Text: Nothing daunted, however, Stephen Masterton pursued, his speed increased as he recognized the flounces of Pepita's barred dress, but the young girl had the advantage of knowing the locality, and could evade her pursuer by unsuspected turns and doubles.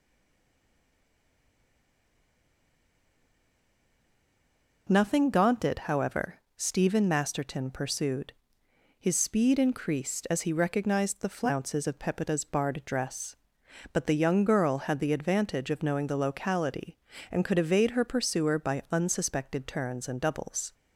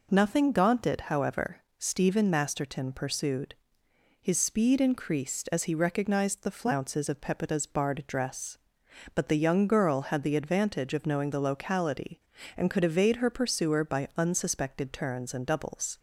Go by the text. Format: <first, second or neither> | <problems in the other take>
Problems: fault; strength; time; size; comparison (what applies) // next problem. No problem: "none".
second | stays silent before the first word; strong; until 4.8 s; 4.8 s long